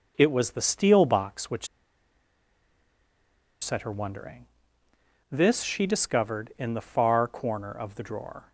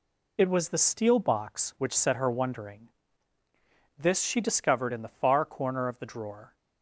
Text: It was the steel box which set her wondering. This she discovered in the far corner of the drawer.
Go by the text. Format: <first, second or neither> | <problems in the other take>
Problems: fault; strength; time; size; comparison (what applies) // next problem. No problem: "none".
second | pauses between "which" and "set"; strong; at 1.6 s; 1.9 s long